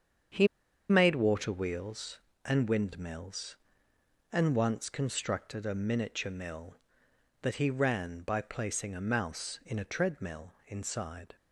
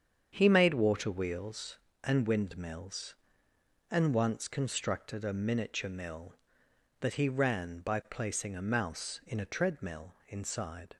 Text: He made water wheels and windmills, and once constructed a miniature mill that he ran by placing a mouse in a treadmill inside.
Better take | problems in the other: second | starts louder than the rest; strong; until 1.7 s; 7.5 dB; strong in the second // pauses between "He" and "made"; at 0.4 s; 0.42 s long

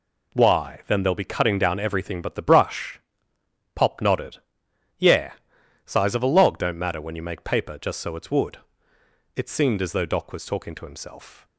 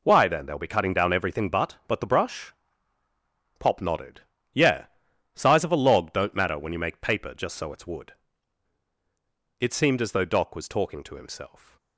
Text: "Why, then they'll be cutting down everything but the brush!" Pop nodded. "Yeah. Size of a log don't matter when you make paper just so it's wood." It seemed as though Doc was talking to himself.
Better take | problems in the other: first | says "but" twice; at 1.8 s

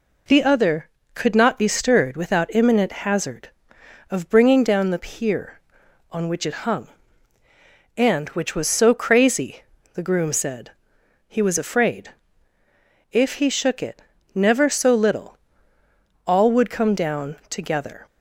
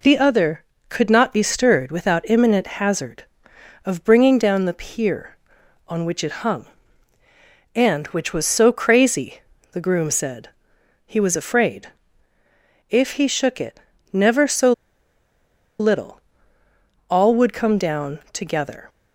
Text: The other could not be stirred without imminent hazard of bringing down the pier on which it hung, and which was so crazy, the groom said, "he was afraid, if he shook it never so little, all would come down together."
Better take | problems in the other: first | pauses between "imminent" and "hazard"; slight; at 2.6 s; 0.16 s long; slight in the first // pauses between "it" and "never"; slight; at 13.7 s; 0.32 s long; slight in the first // pauses between "so" and "little"; at 14.7 s; 1.0 s long

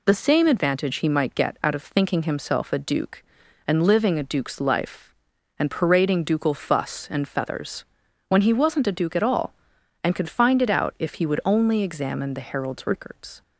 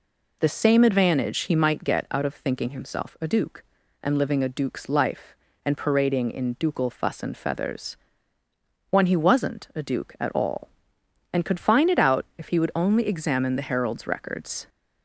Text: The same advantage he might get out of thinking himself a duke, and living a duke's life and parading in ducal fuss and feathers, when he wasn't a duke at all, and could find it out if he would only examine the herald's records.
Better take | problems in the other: second | skips "in"; at 6.2 s

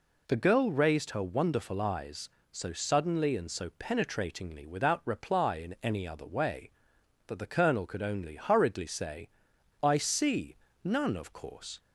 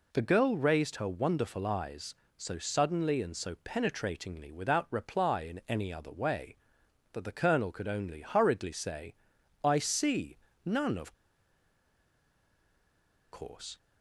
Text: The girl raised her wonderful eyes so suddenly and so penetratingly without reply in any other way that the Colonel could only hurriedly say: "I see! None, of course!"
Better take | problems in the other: first | pauses between "of" and "course"; strong; at 11.1 s; 2.1 s long

